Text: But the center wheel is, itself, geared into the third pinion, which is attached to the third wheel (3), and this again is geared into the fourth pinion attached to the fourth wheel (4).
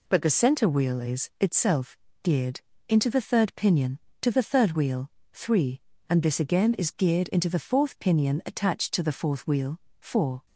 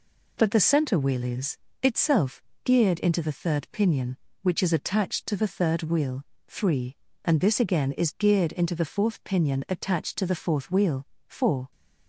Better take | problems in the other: second | pauses between "geared" and "into"; slight; at 2.5 s; 0.28 s long // skips "which is attached"; at 4.0 s

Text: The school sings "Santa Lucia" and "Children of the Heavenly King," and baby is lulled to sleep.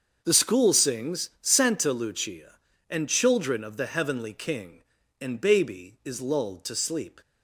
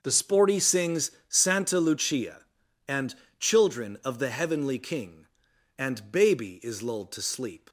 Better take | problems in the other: first | starts louder than the rest; until 1.0 s; 6 dB; also in the first // says "sporty" for "school"; at 0.1 s // pauses between "sings" and "Santa"; slight; at 1.1 s; 0.18 s long // pauses between "and" and "Children"; slight; at 3.1 s; 0.26 s long

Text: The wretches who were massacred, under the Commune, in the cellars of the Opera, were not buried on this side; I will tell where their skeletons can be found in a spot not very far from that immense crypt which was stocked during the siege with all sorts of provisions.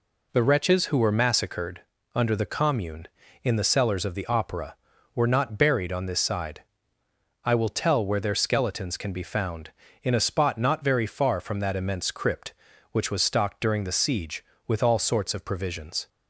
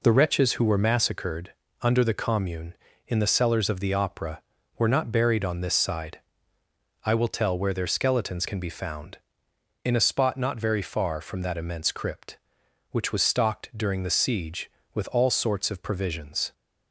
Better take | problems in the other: neither | none

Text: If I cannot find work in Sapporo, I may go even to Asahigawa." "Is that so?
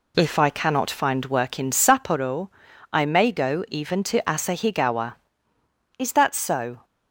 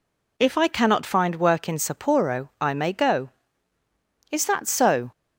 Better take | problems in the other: first | skips "even to Asahigawa"; at 3.8 s

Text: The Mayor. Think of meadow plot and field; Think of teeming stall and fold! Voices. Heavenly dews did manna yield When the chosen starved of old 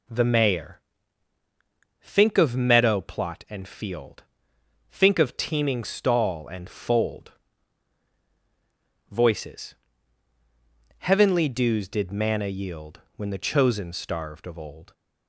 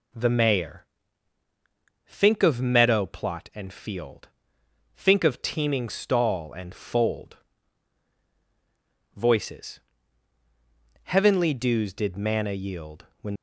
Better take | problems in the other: first | pauses between "yield" and "When"; slight; at 13.0 s; 0.16 s long; slight in the first // stops before "the chosen starved of old"; at 13.3 s

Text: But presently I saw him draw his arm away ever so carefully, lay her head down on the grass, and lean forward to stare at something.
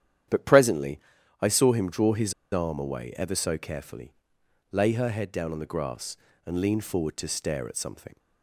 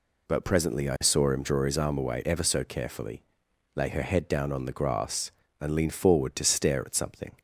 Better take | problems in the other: second | starts louder than the rest; strong; until 1.7 s; 10 dB // pauses between "presently" and "I"; at 0.9 s; 0.42 s long // pauses between "his" and "arm"; slight; at 2.3 s; 0.18 s long

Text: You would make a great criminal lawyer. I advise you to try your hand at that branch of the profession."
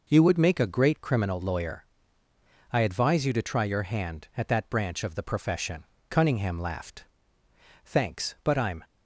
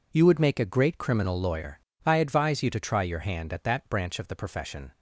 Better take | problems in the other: second | goes on to say "Cunningham laughed Thanks but I'm"; strong; from 6.0 s on; 2.7 s long

